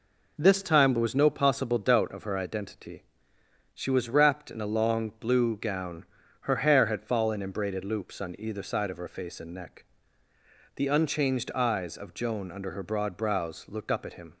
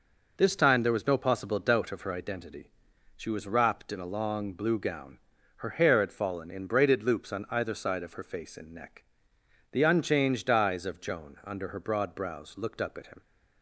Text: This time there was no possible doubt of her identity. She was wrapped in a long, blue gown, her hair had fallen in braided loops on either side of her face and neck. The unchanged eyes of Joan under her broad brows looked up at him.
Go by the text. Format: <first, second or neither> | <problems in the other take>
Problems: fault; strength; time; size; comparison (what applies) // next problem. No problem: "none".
neither | none